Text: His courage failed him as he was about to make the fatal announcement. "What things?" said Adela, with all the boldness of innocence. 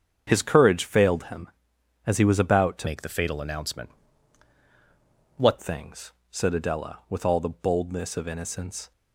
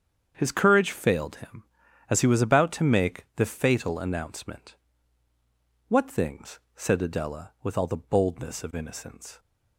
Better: second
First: starts louder than the rest; strong; until 1.3 s; 7.5 dB // changes voice from "make" to "What"; from 2.8 to 5.5 s; 2.7 s long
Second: starts louder than the rest; strong; until 1.3 s; 7.5 dB

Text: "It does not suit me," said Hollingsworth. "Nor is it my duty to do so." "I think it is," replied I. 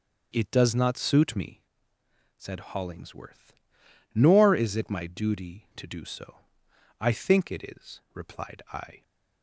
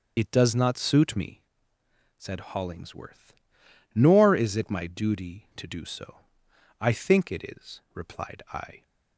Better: first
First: starts louder than the rest; until 1.3 s; 6.5 dB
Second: loses the start of "It"; at 0.1 s; 40 ms // starts louder than the rest; until 1.1 s; 6.5 dB

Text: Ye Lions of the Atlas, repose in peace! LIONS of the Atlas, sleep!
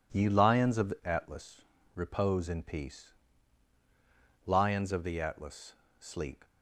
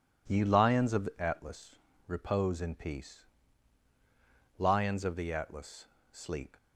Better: neither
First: none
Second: none

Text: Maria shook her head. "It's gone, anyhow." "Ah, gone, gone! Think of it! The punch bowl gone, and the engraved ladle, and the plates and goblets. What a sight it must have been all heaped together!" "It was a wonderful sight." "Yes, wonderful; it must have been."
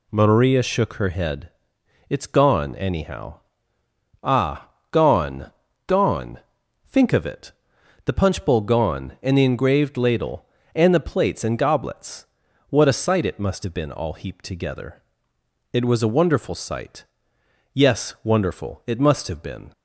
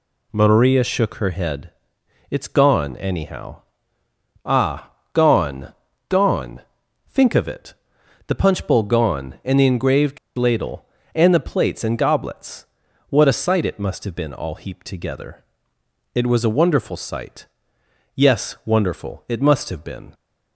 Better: first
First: none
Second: pauses between "engraved" and "ladle"; slight; at 10.1 s; 0.19 s long

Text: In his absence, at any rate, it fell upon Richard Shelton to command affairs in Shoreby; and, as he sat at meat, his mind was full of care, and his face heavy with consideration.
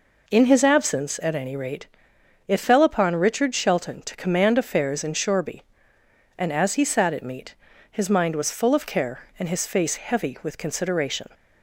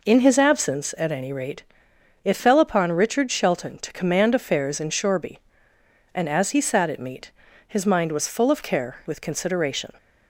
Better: first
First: none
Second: skips "and his face heavy"; at 9.0 s

